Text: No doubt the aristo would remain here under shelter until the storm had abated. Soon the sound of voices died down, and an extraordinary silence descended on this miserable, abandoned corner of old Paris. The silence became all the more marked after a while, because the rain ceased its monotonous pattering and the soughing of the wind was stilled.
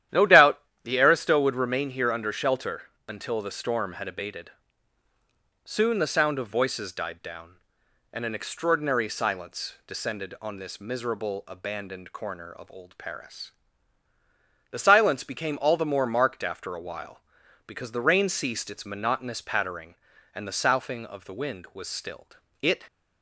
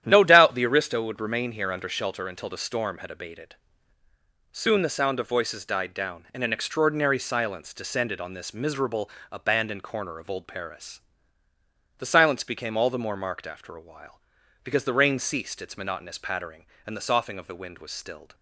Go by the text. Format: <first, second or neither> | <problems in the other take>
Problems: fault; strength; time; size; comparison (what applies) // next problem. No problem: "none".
second | starts louder than the rest; strong; until 1.3 s; 11.5 dB; strong in the second // pauses between "doubt" and "the"; slight; at 0.5 s; 0.24 s long // pauses between "shelter" and "until"; slight; at 2.8 s; 0.24 s long // goes on to say "It"; slight; from 22.6 s on; 0.22 s long